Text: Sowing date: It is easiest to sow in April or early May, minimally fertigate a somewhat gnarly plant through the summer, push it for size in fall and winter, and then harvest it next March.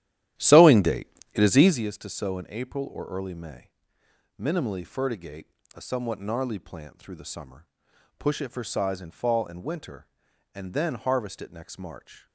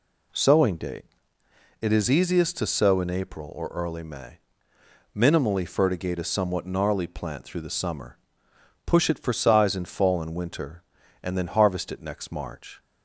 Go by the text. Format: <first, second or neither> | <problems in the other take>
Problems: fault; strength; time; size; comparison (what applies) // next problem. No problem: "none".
second | starts louder than the rest; strong; until 1.8 s; 12.5 dB // pauses between "fertigate" and "a"; slight; at 5.4 s; 0.28 s long